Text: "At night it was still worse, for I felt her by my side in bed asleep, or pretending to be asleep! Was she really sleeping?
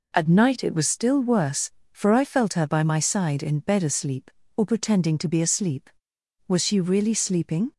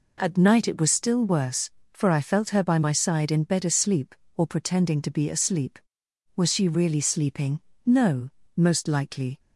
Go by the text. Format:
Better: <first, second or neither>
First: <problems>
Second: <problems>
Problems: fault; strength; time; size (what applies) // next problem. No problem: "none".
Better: first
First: none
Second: goes on to say "No most likely"; from 7.8 s on; 1.5 s long